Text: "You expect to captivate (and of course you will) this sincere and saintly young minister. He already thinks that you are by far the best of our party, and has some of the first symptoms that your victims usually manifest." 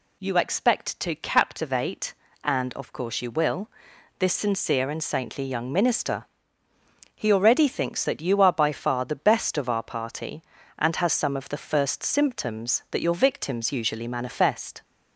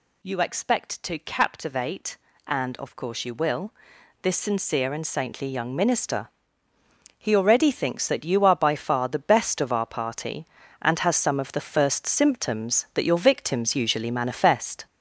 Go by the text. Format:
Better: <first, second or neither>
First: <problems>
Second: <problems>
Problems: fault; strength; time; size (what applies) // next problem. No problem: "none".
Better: first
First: none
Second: gets louder; noticeable; throughout; 6 dB